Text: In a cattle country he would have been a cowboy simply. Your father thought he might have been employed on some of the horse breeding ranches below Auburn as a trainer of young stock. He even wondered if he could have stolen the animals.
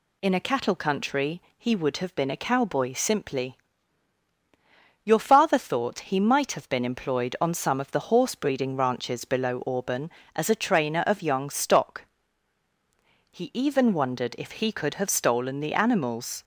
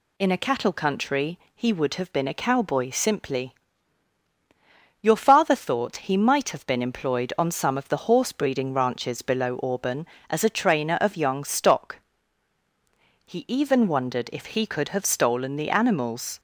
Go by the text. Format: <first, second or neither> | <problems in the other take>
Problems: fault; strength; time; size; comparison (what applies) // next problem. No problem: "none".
neither | pauses between "country" and "he"; slight; the same in both